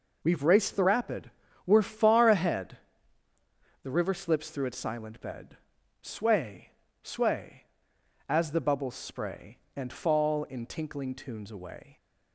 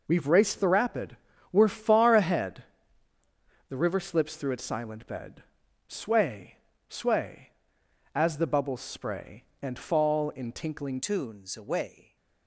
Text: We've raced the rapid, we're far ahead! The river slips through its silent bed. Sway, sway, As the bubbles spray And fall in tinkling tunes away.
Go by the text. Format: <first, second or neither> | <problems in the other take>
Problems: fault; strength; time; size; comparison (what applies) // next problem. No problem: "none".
first | changes voice at "tunes"; from 11.0 s on; 1.1 s long